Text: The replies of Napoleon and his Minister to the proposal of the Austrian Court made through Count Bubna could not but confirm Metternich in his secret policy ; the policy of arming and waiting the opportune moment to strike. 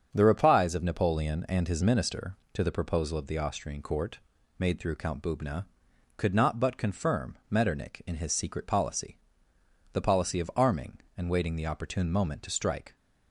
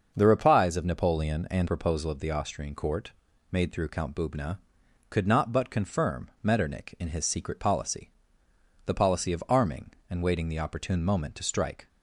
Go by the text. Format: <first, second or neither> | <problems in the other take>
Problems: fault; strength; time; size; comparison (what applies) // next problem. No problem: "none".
first | starts louder than the rest; until 1.1 s; 6.5 dB; also in the first // skips "his Minister to the"; at 1.6 s // pauses between "Court" and "made"; at 3.1 s; 0.40 s long; also in the first